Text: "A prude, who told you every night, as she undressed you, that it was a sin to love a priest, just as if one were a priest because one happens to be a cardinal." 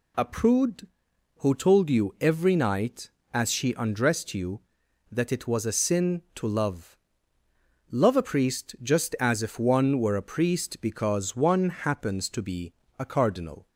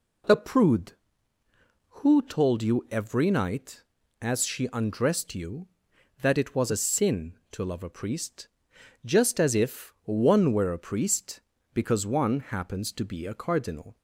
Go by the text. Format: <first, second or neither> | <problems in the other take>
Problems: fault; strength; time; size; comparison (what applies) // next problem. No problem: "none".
second | says "love" twice; at 7.9 s // pauses between "be" and "a"; slight; at 12.7 s; 0.24 s long